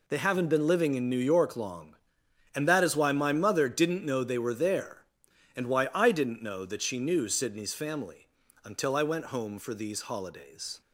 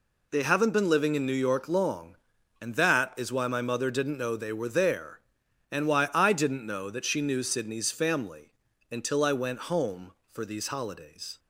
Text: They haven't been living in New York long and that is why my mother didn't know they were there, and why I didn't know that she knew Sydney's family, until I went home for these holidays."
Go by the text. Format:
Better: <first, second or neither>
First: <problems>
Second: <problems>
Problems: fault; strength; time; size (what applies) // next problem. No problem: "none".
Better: neither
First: none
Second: none